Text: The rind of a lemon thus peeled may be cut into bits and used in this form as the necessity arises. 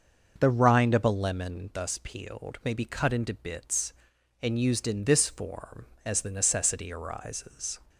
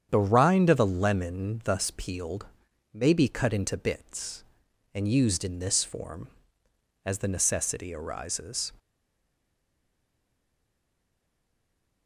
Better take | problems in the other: first | starts louder than the rest; strong; until 1.1 s; 8.5 dB; also in the first // pauses between "peeled" and "may"; noticeable; at 2.4 s; 0.46 s long // stays silent after the last word; strong; from 8.7 s on; 3.3 s long

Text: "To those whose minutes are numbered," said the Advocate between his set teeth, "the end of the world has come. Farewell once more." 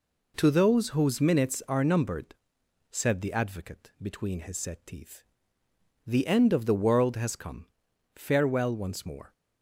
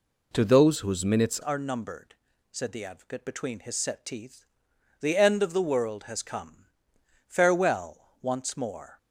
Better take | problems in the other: first | changes voice at "are"; from 1.4 s on; 7.5 s long

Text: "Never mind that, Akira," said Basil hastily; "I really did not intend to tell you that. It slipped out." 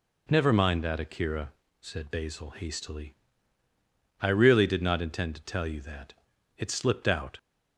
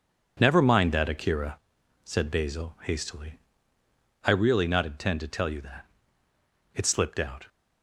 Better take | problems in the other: first | skips "did"; at 4.6 s

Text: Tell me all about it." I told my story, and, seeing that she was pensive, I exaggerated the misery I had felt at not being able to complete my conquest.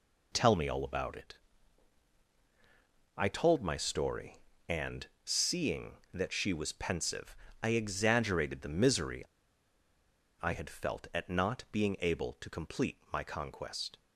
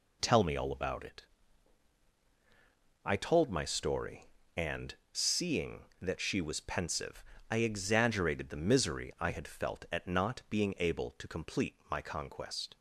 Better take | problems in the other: second | pauses between "misery" and "I"; at 9.2 s; 1.1 s long

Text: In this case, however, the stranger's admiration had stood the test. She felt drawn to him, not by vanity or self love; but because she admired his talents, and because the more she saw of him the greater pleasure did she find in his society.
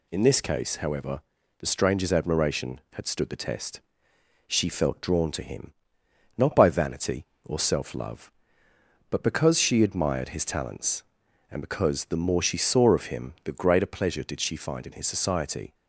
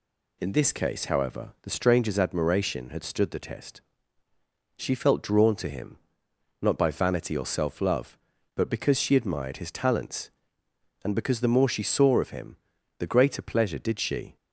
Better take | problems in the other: first | pauses between "him" and "the"; at 12.5 s; 0.44 s long // stops before "find in his society"; at 14.3 s

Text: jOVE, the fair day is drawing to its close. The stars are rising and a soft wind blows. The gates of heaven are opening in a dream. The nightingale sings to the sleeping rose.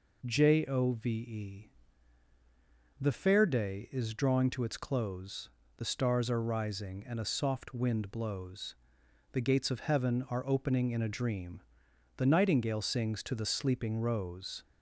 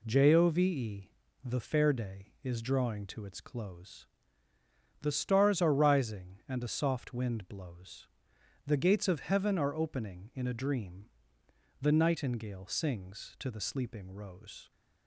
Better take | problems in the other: neither | none

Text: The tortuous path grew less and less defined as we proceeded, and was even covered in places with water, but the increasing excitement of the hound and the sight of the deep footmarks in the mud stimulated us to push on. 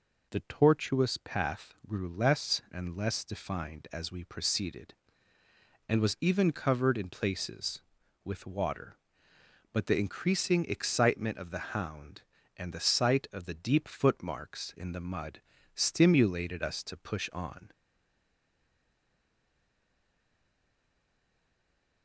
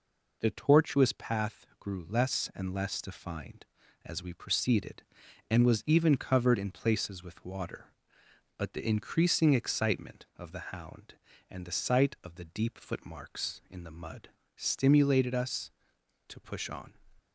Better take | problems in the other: second | pauses between "mud" and "stimulated"; slight; at 15.4 s; 0.34 s long; slight in the second // stays silent after the last word; strong; from 17.7 s on; 4.3 s long

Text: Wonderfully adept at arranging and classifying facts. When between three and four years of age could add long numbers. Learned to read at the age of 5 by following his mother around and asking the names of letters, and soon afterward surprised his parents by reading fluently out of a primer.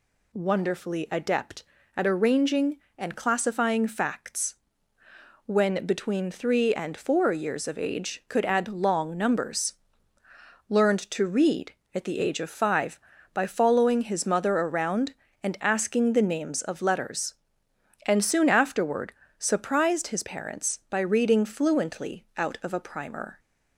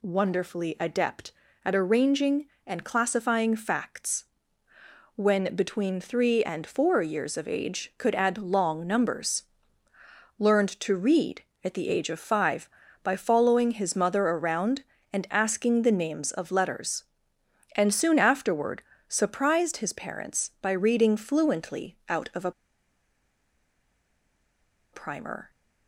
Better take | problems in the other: first | pauses between "afterward" and "surprised"; slight; at 18.8 s; 0.26 s long; slight in the first // pauses between "a" and "primer"; strong; at 22.5 s; 2.4 s long

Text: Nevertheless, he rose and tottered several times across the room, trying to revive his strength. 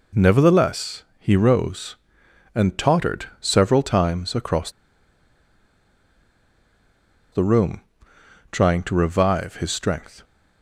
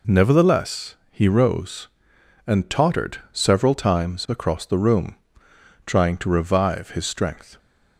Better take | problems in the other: second | pauses between "across" and "the"; strong; at 4.6 s; 2.6 s long

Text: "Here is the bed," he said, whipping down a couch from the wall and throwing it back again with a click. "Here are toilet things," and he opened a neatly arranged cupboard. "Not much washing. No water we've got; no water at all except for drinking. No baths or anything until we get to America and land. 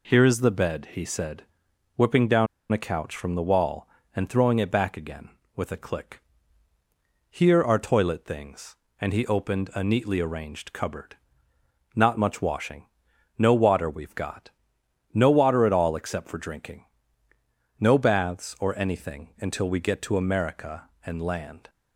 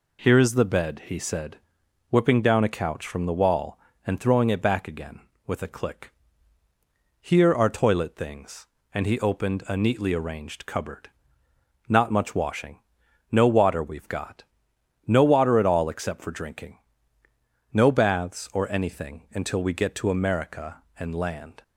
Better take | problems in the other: second | pauses between "down" and "a"; slight; at 2.4 s; 0.24 s long

